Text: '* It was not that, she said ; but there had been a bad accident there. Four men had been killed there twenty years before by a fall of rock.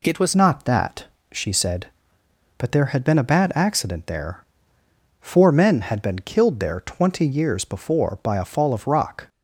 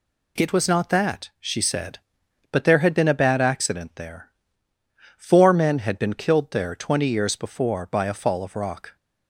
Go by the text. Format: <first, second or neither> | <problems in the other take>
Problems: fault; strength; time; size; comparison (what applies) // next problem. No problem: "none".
second | changes voice at "not"; from 0.3 s on; 8.9 s long